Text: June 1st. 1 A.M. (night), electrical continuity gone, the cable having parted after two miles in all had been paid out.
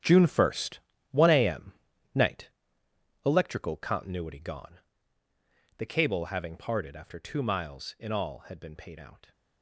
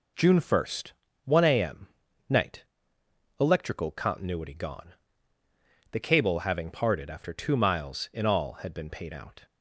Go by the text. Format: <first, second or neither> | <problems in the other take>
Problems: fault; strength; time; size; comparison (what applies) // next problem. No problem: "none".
second | gets quieter; strong; throughout; 12 dB